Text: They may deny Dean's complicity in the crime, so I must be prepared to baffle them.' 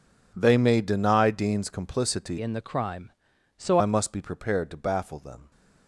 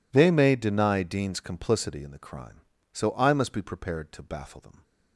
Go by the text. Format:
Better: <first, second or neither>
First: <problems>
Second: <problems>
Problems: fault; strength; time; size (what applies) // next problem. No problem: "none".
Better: second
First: changes voice from "in" to "so"; from 2.3 to 3.7 s; 1.4 s long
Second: none